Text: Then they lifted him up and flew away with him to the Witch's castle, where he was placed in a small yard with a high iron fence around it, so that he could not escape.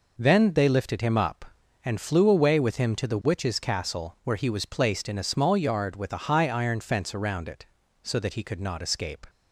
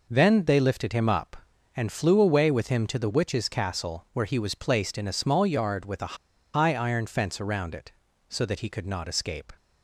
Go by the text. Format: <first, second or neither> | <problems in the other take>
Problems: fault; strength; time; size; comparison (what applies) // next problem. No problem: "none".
first | pauses between "a" and "high"; at 6.1 s; 0.39 s long